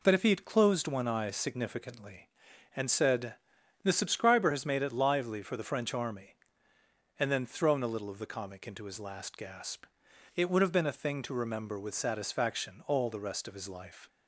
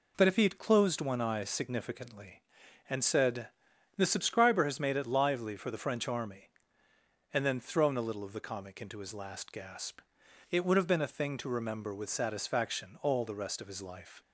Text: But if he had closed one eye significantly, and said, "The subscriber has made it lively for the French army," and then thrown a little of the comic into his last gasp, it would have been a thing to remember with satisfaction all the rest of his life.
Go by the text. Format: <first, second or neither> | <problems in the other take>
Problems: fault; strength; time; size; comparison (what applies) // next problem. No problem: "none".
neither | none